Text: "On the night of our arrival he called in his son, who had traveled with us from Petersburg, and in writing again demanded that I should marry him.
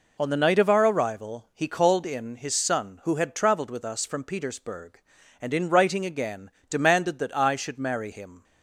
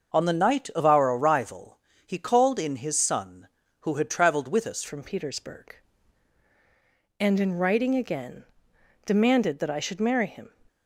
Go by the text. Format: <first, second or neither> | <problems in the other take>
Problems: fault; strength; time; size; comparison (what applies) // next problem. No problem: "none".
first | starts louder than the rest; noticeable; until 1.1 s; 6 dB // pauses between "arrival" and "he"; slight; at 1.7 s; 0.26 s long // changes voice at "from"; from 4.8 s on; 5.7 s long // pauses between "again" and "demanded"; noticeable; at 8.4 s; 0.62 s long; slight in the first